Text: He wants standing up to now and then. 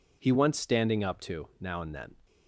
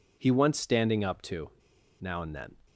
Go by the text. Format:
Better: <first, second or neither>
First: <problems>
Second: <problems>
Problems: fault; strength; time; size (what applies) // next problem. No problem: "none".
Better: first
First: none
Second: pauses between "to" and "now"; noticeable; at 1.5 s; 0.48 s long